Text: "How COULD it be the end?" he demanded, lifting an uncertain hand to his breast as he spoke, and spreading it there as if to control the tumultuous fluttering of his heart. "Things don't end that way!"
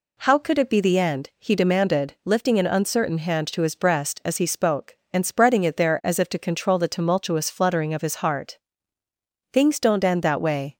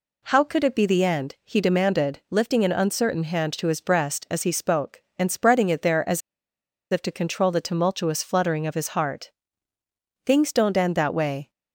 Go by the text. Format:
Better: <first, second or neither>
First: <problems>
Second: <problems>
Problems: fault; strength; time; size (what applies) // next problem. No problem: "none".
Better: first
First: none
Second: pauses between "as" and "if"; noticeable; at 6.2 s; 0.71 s long